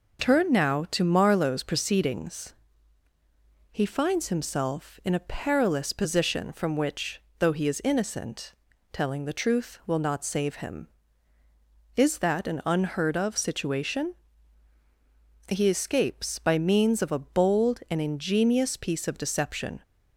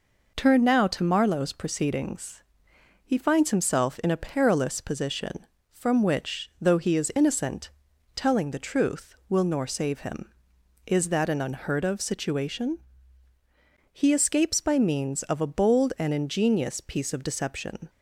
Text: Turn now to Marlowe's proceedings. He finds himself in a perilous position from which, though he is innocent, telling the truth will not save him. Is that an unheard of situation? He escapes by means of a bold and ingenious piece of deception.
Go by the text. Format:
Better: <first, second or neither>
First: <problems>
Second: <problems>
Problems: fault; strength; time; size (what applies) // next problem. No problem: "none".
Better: first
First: none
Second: says "nor" for "not"; at 9.4 s